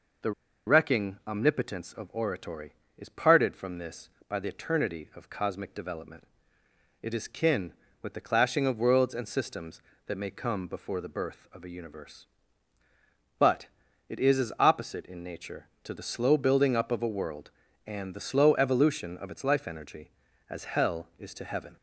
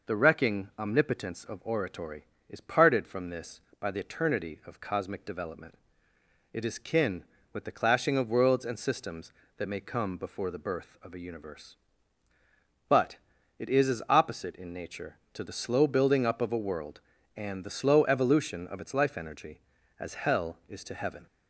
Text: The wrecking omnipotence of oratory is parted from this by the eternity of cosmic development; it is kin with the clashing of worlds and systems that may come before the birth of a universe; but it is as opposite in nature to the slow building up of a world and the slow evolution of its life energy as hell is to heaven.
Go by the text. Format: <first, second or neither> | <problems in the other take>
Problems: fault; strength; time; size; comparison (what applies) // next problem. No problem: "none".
second | pauses between "The" and "wrecking"; slight; at 0.3 s; 0.35 s long // pauses between "but" and "it"; at 13.6 s; 0.40 s long; also in the second